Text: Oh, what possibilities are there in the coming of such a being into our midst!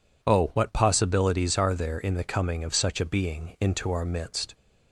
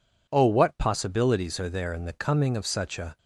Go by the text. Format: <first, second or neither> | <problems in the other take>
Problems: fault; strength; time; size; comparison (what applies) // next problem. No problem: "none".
first | stops before "being into our midst"; at 3.1 s